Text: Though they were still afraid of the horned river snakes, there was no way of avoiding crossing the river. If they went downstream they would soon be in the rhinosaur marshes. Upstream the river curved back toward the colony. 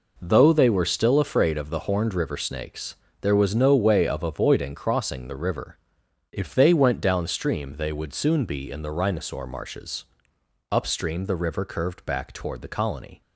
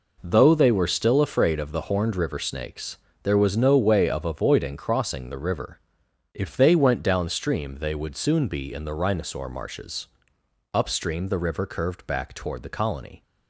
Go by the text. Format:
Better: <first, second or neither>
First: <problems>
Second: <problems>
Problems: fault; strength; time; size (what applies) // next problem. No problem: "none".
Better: neither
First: none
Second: none